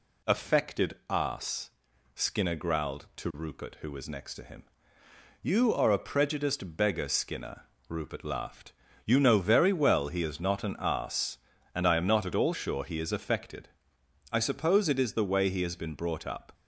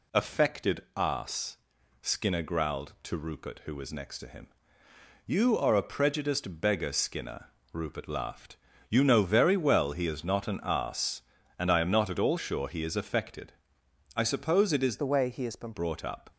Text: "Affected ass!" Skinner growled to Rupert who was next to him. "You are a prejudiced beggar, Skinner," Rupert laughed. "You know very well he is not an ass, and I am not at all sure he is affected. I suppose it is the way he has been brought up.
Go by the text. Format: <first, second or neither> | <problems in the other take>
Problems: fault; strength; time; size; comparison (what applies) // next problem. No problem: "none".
first | changes voice from "the" to "been"; from 14.9 to 15.7 s; 0.8 s long